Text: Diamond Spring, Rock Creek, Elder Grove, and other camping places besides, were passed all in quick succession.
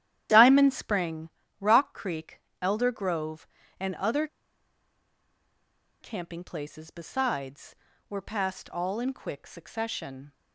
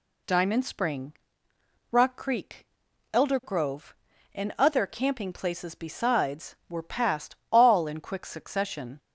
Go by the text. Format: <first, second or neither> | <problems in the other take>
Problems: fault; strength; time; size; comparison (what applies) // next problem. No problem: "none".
second | starts louder than the rest; strong; until 1.6 s; 11.5 dB // pauses between "other" and "camping"; strong; at 4.2 s; 1.7 s long